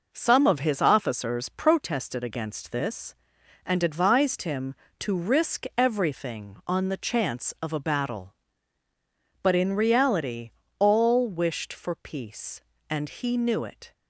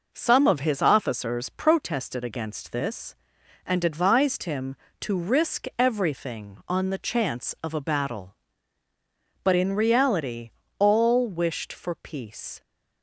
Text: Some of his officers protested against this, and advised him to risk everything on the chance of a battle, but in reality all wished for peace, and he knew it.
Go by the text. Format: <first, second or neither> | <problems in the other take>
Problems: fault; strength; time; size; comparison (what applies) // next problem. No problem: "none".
first | pauses between "reality" and "all"; slight; at 10.5 s; 0.28 s long; slight in the first // stops before "and he knew it"; at 12.6 s